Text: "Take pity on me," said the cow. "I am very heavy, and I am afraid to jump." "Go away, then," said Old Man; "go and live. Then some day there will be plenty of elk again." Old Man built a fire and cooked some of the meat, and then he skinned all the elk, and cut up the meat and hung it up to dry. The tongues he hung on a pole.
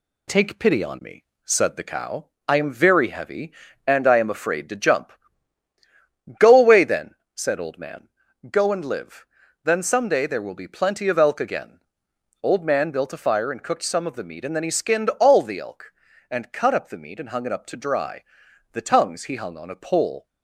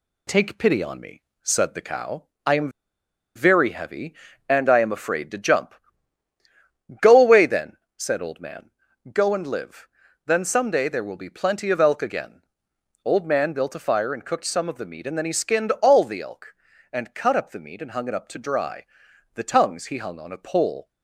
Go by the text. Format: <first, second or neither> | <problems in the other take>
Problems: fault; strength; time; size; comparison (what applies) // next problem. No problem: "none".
first | pauses between "am" and "very"; noticeable; at 2.7 s; 0.65 s long